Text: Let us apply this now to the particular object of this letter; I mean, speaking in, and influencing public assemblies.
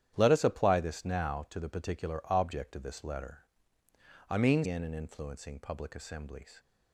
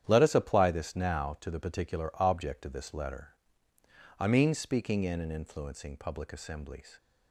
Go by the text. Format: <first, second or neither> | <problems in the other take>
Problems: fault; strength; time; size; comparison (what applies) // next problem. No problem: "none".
second | starts louder than the rest; strong; until 1.1 s; 10 dB; strong in the second // skips "speaking"; at 4.6 s